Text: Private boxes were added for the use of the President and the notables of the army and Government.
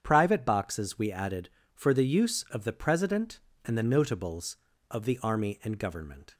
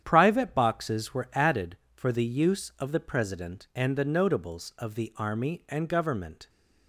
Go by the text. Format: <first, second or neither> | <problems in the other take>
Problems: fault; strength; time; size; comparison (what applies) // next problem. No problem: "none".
second | starts louder than the rest; strong; until 1.0 s; 8.5 dB; strong in the second // says "we" for "were"; at 0.9 s